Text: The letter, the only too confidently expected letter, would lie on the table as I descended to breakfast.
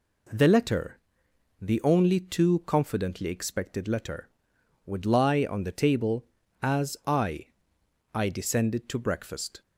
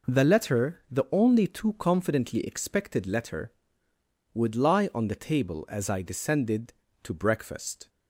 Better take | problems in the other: second | says "I" twice; at 8.1 s

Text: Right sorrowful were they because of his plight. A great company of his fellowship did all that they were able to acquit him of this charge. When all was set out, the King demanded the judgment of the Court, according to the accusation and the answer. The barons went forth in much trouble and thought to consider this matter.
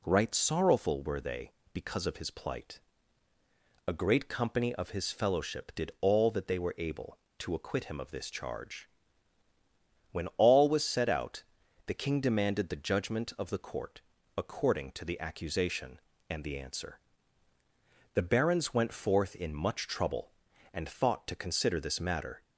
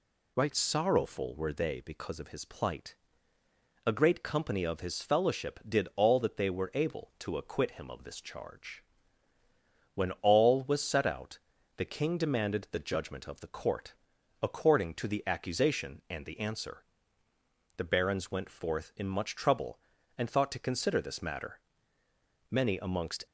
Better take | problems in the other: first | goes on to say "Many amongst"; noticeable; from 22.4 s on; 0.76 s long

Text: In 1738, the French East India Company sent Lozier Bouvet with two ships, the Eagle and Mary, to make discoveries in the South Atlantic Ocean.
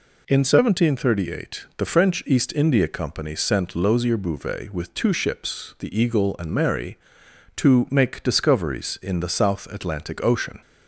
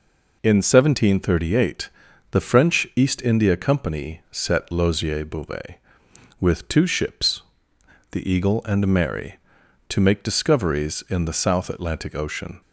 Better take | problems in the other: first | says "set" for "sent"; at 4.3 s

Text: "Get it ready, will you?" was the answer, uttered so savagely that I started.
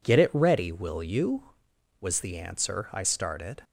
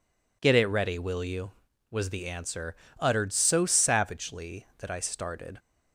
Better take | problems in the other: second | skips "uttered so savagely that"; at 2.9 s

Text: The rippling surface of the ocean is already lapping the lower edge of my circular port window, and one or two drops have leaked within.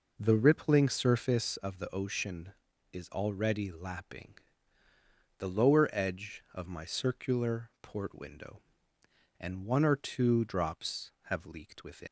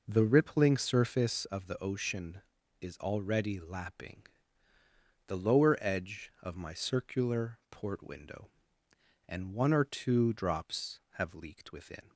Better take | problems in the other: second | pauses between "lapping" and "the"; at 4.3 s; 1.0 s long; also in the second // leaves "within" unfinished; at 12.0 s; 165 ms

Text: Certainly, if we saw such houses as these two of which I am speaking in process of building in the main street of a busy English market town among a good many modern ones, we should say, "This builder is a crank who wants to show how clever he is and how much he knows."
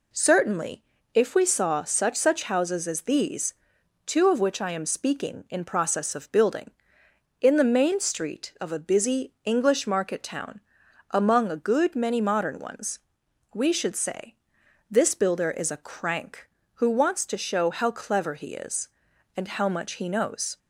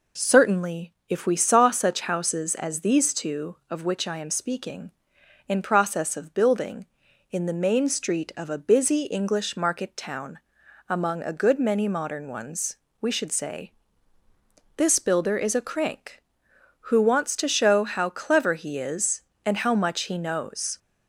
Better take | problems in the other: second | says "such" twice; at 2.1 s // pauses between "these" and "two"; noticeable; at 3.5 s; 0.50 s long // pauses between "town" and "among"; noticeable; at 10.5 s; 0.52 s long; noticeable in the second

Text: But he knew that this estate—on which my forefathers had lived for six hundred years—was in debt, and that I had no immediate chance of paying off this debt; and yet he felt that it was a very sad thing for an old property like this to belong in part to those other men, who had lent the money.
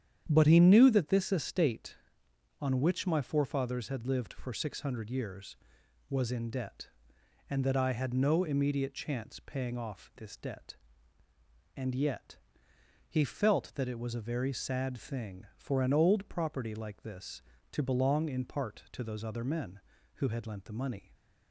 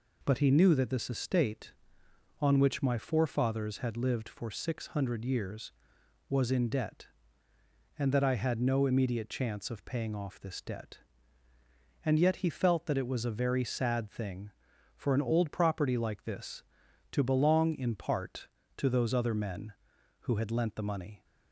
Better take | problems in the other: second | starts louder than the rest; strong; until 1.3 s; 9 dB // skips "of"; at 9.3 s // pauses between "yet" and "he"; noticeable; at 12.3 s; 0.72 s long

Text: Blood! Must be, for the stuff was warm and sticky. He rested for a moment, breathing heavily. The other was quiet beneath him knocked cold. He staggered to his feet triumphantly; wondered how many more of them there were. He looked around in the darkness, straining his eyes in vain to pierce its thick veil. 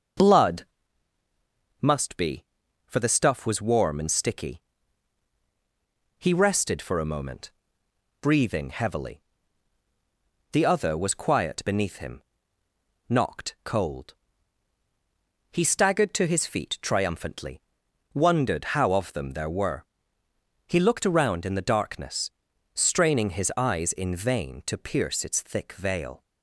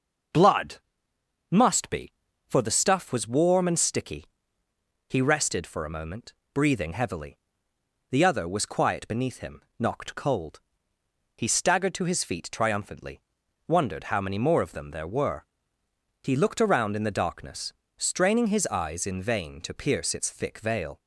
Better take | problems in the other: second | starts louder than the rest; noticeable; until 2.3 s; 6 dB // pauses between "him" and "knocked"; noticeable; at 12.2 s; 0.86 s long; slight in the second // skips "many more"; at 18.9 s

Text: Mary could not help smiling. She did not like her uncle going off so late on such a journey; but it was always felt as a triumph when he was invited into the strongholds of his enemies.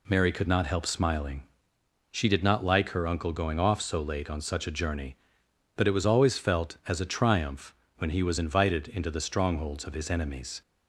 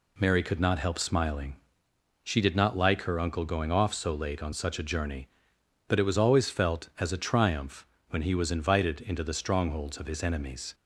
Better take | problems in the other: neither | pauses between "triumph" and "when"; slight; the same in both

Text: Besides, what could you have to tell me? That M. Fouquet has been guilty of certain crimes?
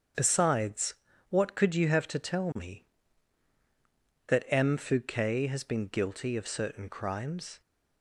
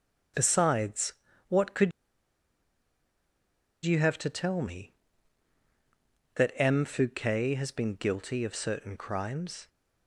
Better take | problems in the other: first | starts louder than the rest; strong; until 1.6 s; 7.5 dB; strong in the first // pauses between "could" and "you"; strong; at 1.9 s; 1.9 s long

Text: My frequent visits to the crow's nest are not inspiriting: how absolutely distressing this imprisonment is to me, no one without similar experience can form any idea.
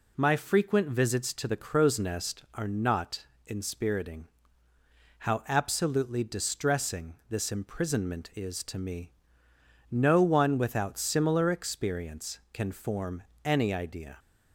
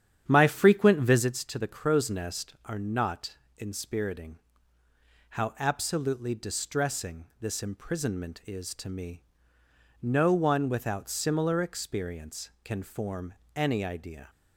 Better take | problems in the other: first | starts louder than the rest; strong; until 1.3 s; 9 dB // pauses between "not" and "inspiriting"; slight; at 3.3 s; 0.22 s long; slight in the first // pauses between "distressing" and "this"; slight; at 7.2 s; 0.16 s long; slight in the first // pauses between "form" and "any"; slight; at 13.3 s; 0.20 s long; slight in the first

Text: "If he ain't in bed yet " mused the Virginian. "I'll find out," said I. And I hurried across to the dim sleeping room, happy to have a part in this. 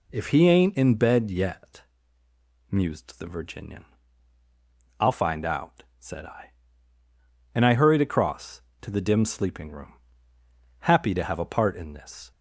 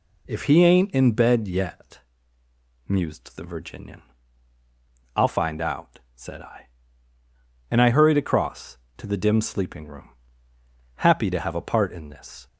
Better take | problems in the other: neither | none

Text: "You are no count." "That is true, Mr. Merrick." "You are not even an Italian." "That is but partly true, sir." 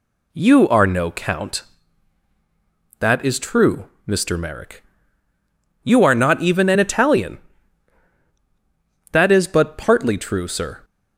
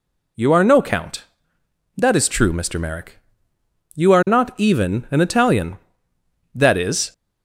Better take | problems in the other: first | stops before "but partly true sir"; at 7.1 s

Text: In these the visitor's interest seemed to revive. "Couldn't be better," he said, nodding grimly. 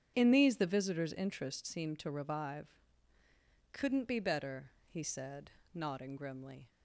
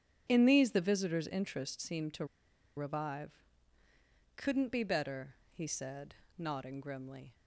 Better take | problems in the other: first | starts louder than the rest; strong; until 1.2 s; 9 dB; strong in the first // pauses between "to" and "revive"; noticeable; at 2.2 s; 0.50 s long

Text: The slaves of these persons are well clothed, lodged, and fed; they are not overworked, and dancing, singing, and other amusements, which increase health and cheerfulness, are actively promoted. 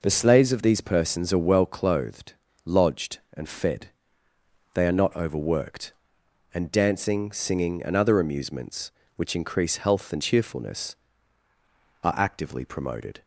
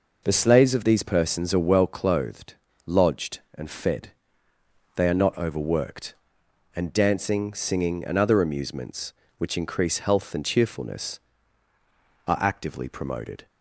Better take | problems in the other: neither | none

